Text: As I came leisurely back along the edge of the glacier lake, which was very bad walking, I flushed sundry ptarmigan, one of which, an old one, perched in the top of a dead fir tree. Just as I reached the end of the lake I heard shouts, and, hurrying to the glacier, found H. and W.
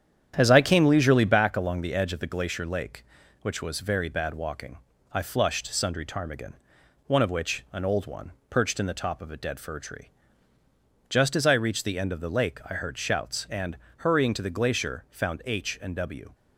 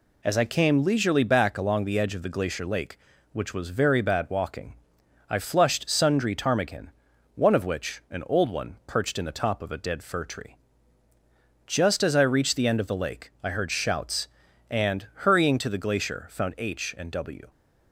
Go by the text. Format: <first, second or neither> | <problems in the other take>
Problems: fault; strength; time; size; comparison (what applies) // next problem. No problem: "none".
second | starts louder than the rest; strong; until 1.4 s; 9.5 dB